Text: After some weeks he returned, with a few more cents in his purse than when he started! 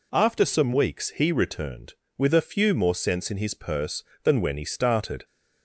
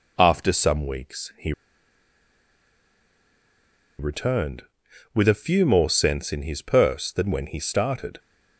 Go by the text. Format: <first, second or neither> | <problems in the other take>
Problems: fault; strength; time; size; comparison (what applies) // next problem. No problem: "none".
first | pauses between "he" and "returned"; strong; at 1.5 s; 2.4 s long